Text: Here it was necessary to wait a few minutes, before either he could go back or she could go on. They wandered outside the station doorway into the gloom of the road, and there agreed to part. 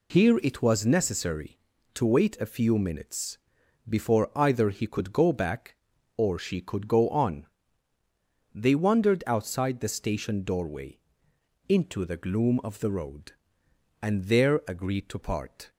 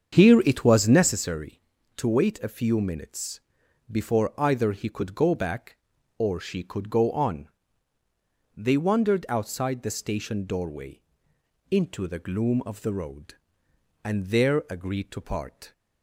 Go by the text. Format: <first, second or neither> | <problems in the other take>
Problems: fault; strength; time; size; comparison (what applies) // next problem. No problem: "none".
first | starts louder than the rest; until 1.2 s; 7 dB // pauses between "doorway" and "into"; noticeable; at 11.0 s; 0.70 s long; noticeable in the first